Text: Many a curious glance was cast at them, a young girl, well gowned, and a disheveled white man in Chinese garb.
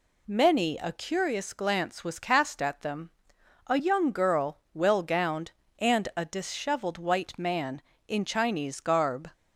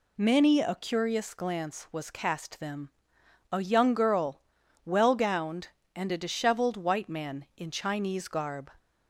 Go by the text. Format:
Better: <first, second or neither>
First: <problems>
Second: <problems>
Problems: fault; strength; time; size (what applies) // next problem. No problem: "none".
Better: first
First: none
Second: skips "at"; at 2.5 s